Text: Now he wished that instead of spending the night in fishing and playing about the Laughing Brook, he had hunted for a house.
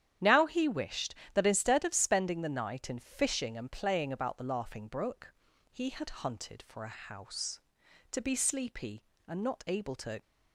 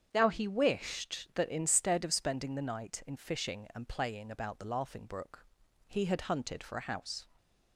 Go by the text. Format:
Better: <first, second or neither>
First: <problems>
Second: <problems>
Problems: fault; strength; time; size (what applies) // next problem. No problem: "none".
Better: second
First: starts louder than the rest; strong; until 1.4 s; 10 dB // goes on to say "To be sleepy and not able to"; strong; from 8.1 s on; 2.0 s long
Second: starts louder than the rest; strong; until 1.1 s; 8 dB